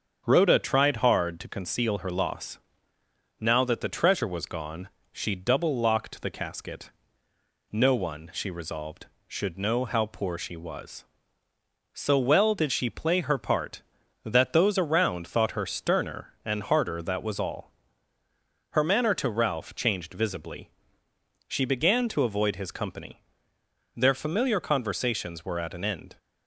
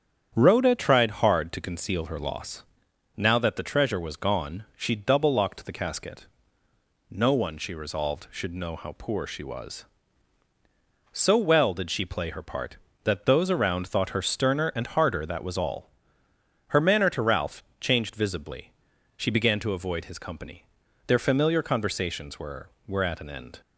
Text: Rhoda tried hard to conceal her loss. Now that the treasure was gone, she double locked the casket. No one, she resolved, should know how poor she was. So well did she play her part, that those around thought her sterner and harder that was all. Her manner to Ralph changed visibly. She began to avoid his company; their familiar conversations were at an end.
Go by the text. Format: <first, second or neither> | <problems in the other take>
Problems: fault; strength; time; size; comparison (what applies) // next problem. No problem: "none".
first | starts louder than the rest; strong; until 1.3 s; 8.5 dB; strong in the first // pauses between "Ralph" and "changed"; slight; at 17.6 s; 0.16 s long // says "were" twice; at 22.8 s